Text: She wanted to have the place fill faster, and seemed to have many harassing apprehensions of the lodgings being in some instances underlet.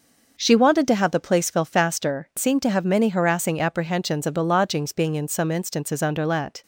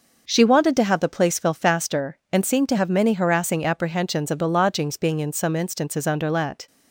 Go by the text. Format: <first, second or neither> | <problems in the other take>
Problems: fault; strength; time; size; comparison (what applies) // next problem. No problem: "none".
second | skips "and"; at 2.3 s